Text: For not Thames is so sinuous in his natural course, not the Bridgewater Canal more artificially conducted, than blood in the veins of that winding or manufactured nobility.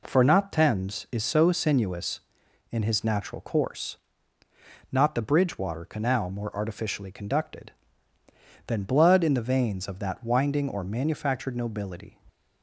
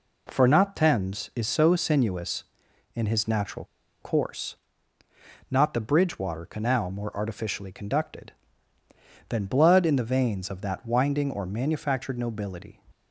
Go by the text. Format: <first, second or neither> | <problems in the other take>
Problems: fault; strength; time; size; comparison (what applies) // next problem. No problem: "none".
first | pauses between "natural" and "course"; at 3.6 s; 0.37 s long